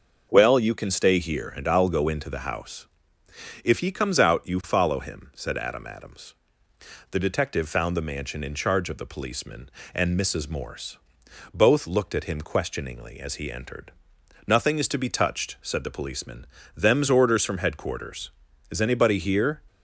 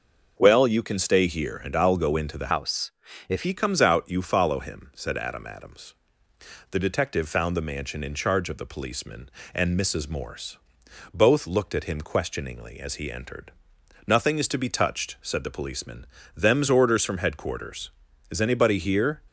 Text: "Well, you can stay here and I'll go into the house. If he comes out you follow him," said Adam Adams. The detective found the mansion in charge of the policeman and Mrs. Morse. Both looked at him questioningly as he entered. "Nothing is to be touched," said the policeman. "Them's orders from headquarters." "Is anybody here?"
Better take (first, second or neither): first